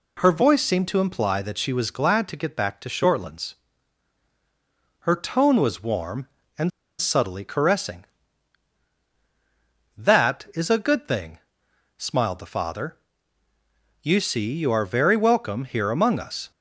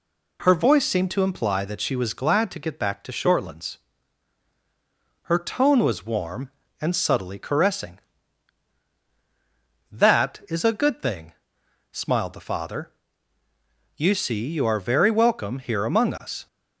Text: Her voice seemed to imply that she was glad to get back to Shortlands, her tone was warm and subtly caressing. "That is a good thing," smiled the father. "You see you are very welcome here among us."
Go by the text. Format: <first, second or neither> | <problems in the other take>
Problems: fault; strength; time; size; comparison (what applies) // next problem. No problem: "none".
second | pauses between "and" and "subtly"; slight; at 6.7 s; 0.30 s long